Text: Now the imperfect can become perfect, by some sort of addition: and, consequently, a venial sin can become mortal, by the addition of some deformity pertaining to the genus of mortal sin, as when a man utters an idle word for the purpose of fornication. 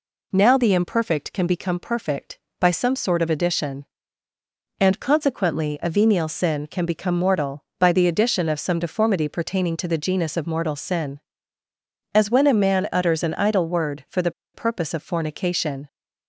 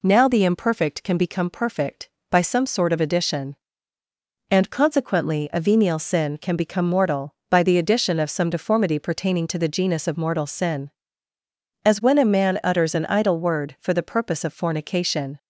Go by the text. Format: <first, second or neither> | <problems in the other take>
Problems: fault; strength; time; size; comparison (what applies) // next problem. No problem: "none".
second | pauses between "the" and "purpose"; slight; at 14.3 s; 0.23 s long